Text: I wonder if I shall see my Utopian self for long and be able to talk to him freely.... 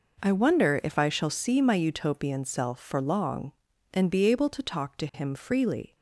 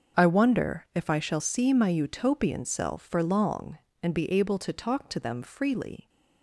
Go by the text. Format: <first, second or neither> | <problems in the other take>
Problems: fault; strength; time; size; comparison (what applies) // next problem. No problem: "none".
first | starts louder than the rest; until 1.2 s; 6.5 dB // says "them" for "him"; at 5.1 s